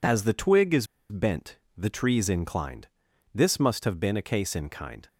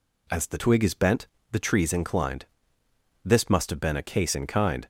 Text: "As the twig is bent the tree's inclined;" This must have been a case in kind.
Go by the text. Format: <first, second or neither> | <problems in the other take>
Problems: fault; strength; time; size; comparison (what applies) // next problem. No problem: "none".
second | pauses between "is" and "bent"; slight; at 0.8 s; 0.24 s long // pauses between "bent" and "the"; slight; at 1.5 s; 0.20 s long; slight in the second